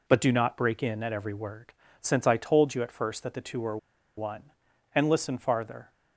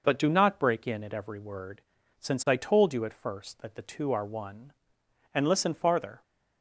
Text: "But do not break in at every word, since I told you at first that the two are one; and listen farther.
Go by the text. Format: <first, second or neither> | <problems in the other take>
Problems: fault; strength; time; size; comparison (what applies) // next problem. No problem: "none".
second | pauses between "are" and "one"; at 3.7 s; 0.40 s long